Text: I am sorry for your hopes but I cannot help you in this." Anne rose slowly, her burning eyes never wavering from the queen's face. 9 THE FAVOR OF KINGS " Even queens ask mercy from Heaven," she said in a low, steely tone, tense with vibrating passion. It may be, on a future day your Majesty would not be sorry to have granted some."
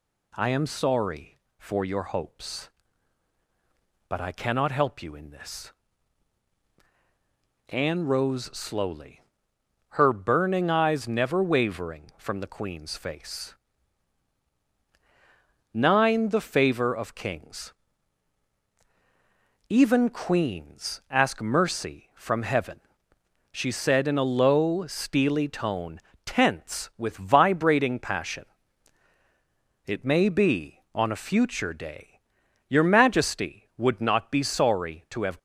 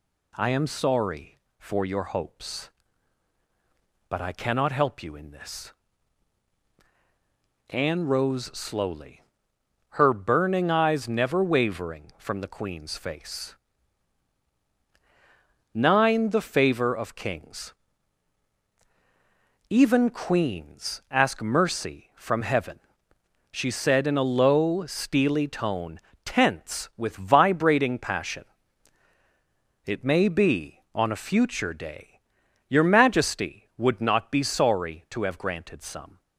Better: second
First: pauses between "day" and "your"; noticeable; at 32.1 s; 0.48 s long // stops before "granted some"; at 35.3 s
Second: pauses between "day" and "your"; noticeable; at 32.1 s; 0.48 s long

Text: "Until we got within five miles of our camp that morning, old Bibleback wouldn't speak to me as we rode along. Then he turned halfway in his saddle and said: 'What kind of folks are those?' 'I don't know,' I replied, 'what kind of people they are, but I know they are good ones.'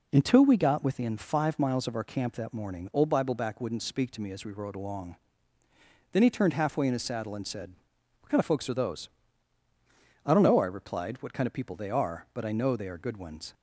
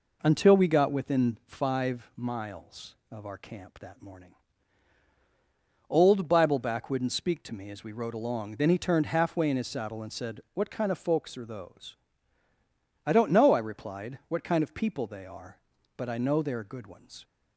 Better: neither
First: none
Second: none

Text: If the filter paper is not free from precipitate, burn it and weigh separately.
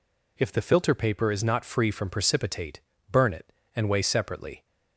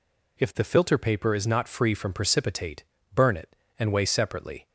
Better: neither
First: none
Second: none

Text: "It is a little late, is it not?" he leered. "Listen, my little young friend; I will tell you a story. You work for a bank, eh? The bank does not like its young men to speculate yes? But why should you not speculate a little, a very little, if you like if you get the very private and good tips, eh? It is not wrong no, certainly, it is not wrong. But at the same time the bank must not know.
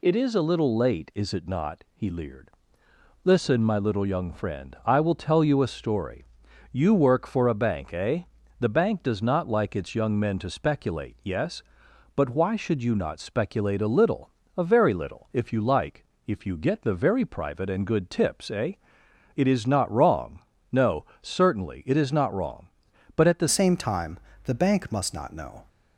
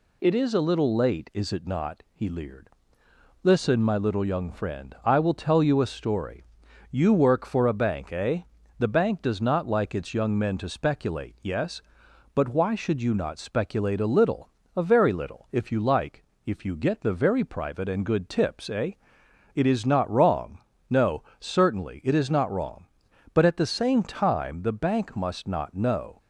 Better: second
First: pauses between "like" and "if"; slight; at 16.0 s; 0.22 s long // pauses between "wrong" and "no"; slight; at 20.3 s; 0.32 s long // changes voice at "same"; from 23.4 s on; 2.2 s long // pauses between "time" and "the"; slight; at 24.1 s; 0.24 s long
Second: pauses between "like" and "if"; slight; at 16.2 s; 0.22 s long // pauses between "wrong" and "no"; slight; at 20.5 s; 0.30 s long

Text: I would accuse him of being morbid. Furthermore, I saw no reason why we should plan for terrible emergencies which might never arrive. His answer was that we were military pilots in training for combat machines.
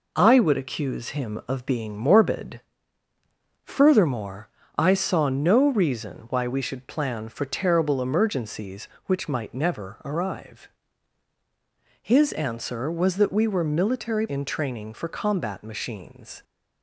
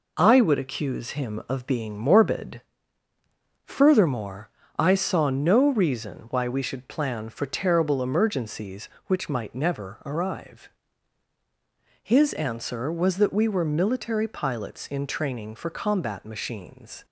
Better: second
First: skips "pilots"; at 14.2 s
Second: none

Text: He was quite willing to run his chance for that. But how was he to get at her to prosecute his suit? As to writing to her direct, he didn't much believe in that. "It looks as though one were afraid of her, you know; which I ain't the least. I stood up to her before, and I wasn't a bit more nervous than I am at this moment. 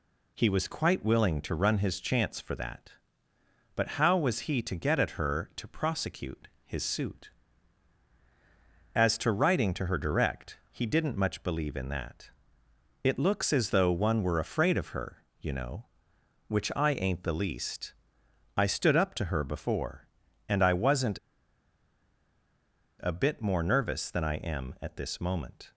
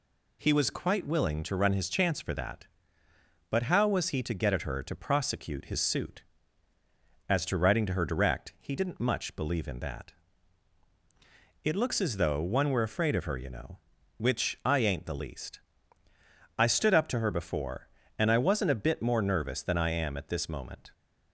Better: second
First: pauses between "prosecute" and "his"; slight; at 6.4 s; 0.16 s long // pauses between "wasn't" and "a"; strong; at 21.1 s; 1.8 s long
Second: none

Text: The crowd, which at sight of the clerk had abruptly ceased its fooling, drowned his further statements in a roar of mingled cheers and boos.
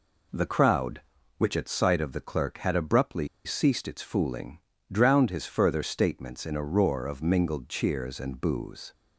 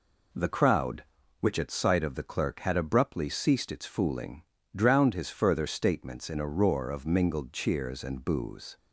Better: second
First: pauses between "abruptly" and "ceased"; slight; at 3.2 s; 0.18 s long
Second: none

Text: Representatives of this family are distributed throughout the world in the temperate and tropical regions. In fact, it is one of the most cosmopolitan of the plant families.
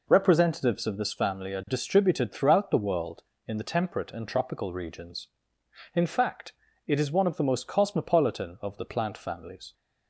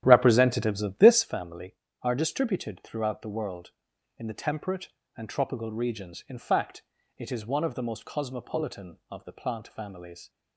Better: first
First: none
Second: starts louder than the rest; strong; until 1.3 s; 11.5 dB

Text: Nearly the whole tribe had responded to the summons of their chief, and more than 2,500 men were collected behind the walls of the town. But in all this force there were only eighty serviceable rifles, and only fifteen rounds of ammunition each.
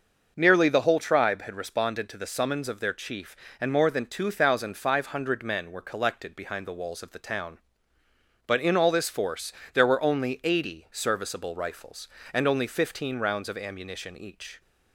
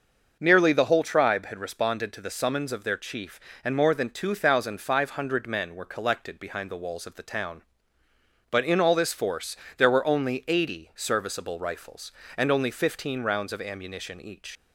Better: first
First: starts louder than the rest; until 1.3 s; 6.5 dB // pauses between "force" and "there"; slight; at 9.5 s; 0.22 s long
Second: starts louder than the rest; until 1.4 s; 6.5 dB // pauses between "force" and "there"; slight; at 9.5 s; 0.22 s long // leaves "each" unfinished; at 14.5 s; 85 ms

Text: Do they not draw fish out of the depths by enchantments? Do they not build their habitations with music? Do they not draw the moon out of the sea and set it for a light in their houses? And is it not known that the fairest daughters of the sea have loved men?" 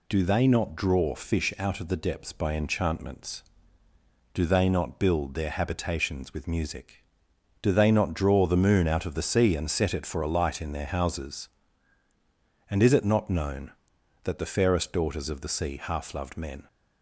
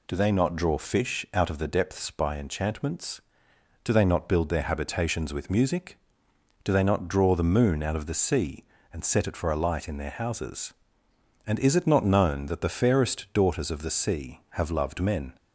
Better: second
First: says "half" for "have"; at 15.8 s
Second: none

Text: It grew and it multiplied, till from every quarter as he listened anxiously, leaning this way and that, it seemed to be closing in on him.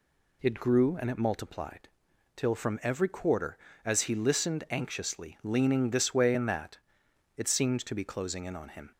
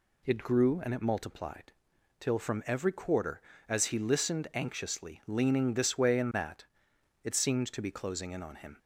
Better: neither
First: none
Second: none

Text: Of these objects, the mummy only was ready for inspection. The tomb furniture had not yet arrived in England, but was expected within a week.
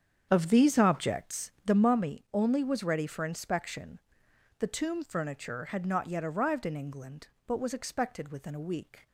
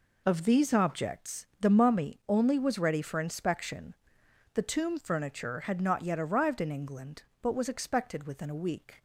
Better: second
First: starts louder than the rest; strong; until 1.8 s; 8 dB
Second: none

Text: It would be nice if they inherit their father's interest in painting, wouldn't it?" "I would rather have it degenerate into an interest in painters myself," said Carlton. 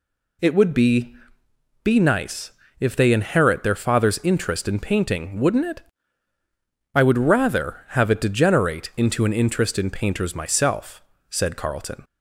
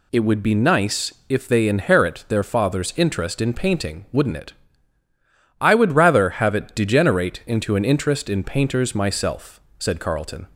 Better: second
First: says "be" twice; at 1.8 s // pauses between "nice" and "if"; slight; at 2.5 s; 0.28 s long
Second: none

